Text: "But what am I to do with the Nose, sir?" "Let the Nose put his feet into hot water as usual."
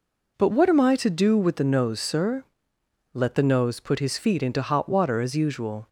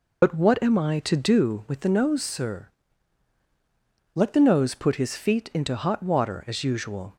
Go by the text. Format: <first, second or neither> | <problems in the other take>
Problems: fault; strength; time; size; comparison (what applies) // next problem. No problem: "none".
first | loses the start of "But"; at 0.2 s; 90 ms